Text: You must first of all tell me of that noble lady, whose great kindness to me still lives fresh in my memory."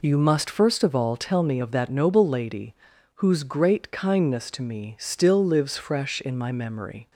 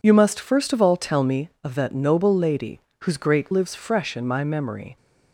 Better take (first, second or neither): first